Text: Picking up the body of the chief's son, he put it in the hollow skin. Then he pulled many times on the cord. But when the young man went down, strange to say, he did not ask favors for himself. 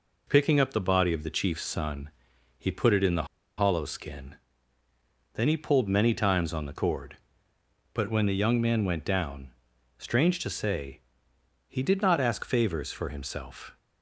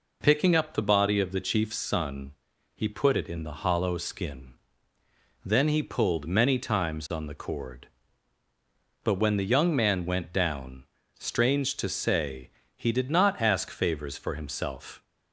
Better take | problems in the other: second | pauses between "the" and "hollow"; slight; at 3.2 s; 0.33 s long

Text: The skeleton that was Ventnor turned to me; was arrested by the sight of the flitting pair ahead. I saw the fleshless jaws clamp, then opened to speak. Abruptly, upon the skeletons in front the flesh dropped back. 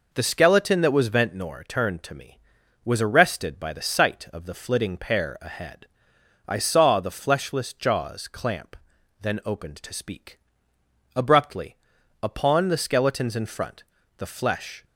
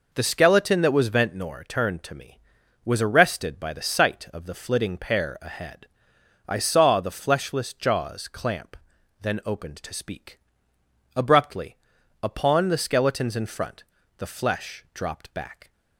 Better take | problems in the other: second | pauses between "front" and "the"; slight; at 13.8 s; 0.34 s long; slight in the second // stops before "dropped back"; at 14.8 s

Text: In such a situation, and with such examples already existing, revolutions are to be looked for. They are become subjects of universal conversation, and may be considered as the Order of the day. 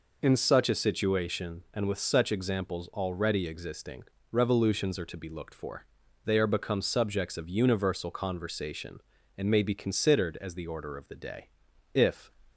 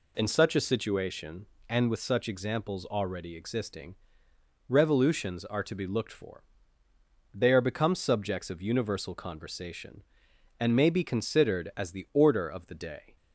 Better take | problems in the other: second | goes on to say "If"; slight; from 11.9 s on; 0.38 s long

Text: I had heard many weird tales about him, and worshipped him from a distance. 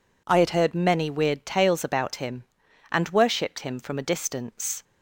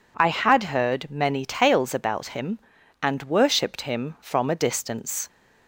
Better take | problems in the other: first | skips "weird"; at 1.4 s

